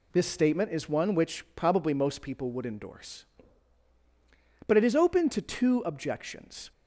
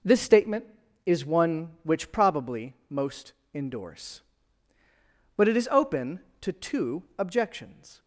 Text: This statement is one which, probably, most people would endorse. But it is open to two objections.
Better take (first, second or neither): first